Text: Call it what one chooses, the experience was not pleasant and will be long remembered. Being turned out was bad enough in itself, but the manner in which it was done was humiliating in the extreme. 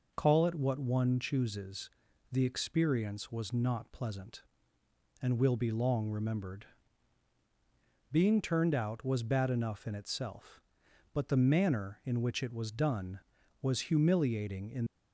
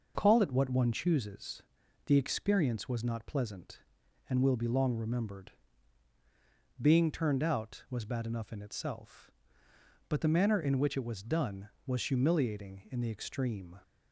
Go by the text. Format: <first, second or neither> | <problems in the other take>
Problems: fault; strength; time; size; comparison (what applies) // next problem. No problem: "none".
second | stops before "the extreme"; at 14.8 s